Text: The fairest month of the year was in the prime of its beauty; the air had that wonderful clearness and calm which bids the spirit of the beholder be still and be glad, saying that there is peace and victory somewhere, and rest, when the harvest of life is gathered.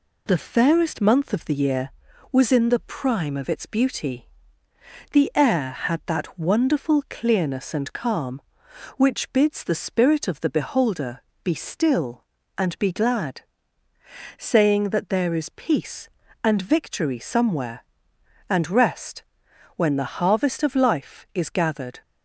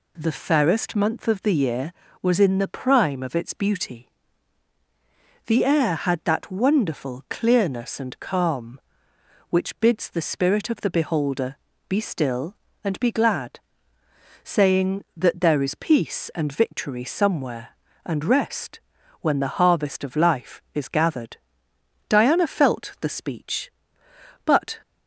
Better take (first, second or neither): first